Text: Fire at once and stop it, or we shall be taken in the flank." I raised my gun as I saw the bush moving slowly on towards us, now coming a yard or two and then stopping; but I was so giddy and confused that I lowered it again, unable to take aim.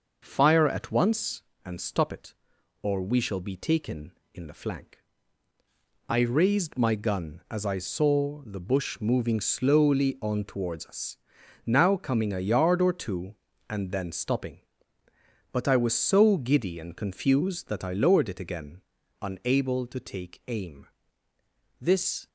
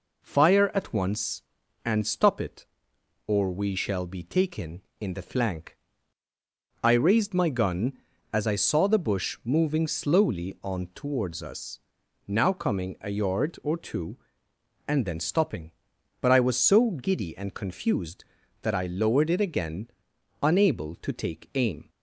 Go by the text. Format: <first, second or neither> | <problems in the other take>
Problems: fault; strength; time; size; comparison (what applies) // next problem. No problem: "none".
second | goes on to say "This"; slight; from 21.8 s on; 0.46 s long